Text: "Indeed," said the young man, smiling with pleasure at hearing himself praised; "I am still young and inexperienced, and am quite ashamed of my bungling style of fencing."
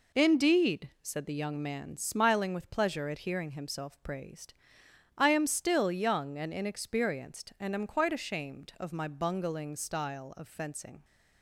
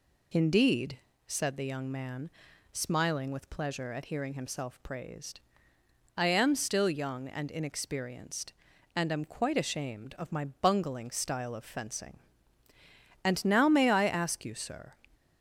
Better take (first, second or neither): first